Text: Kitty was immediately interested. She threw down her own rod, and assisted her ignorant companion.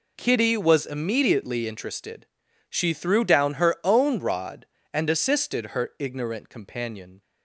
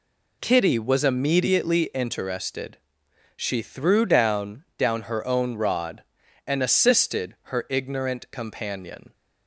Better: first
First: none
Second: says "down" twice; at 4.7 s

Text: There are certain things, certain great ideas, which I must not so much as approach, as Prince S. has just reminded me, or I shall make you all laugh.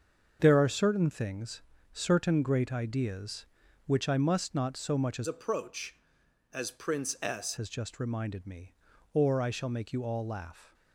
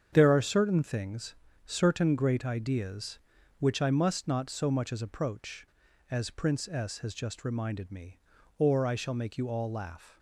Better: second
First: starts louder than the rest; until 1.4 s; 7 dB // changes voice from "approach" to "S"; from 5.2 to 7.5 s; 2.3 s long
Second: starts louder than the rest; strong; until 1.1 s; 7.5 dB

